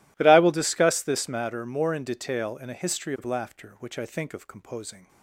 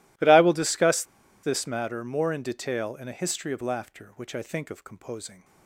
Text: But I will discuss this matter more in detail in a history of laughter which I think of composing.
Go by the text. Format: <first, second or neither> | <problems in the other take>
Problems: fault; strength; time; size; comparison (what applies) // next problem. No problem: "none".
first | pauses between "discuss" and "this"; at 1.0 s; 0.39 s long